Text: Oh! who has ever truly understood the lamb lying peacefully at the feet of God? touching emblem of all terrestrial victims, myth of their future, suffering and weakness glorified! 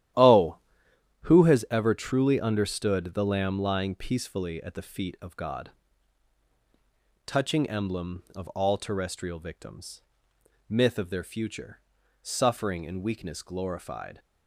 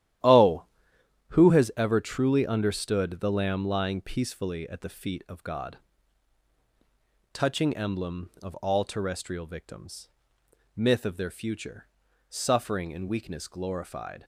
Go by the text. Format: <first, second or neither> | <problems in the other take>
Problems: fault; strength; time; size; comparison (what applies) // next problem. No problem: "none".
neither | starts louder than the rest; strong; the same in both